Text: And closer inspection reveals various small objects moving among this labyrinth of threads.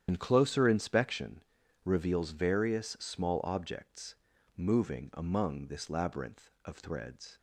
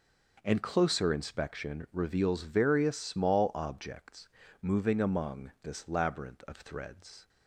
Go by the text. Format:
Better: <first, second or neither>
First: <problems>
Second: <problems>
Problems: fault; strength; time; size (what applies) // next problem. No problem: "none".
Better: second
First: loses the start of "And"; at 0.0 s; 70 ms // starts louder than the rest; strong; until 1.0 s; 9.5 dB // pauses between "inspection" and "reveals"; at 1.4 s; 0.40 s long // pauses between "objects" and "moving"; at 4.1 s; 0.40 s long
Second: pauses between "objects" and "moving"; slight; at 4.2 s; 0.32 s long